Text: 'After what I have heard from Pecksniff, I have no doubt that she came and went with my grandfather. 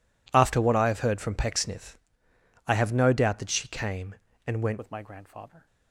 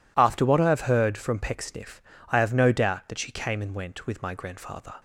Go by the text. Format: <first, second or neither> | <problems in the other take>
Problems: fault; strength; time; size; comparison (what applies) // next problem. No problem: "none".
second | changes voice at "with"; from 4.7 s on; 0.9 s long